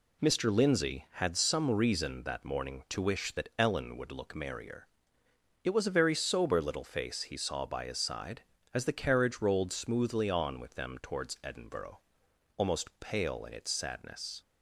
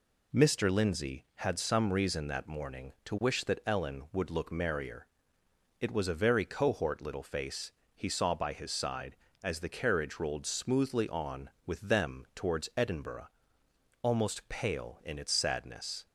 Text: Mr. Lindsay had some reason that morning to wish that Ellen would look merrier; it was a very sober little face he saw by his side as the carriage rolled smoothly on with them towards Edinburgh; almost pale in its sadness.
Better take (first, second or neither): first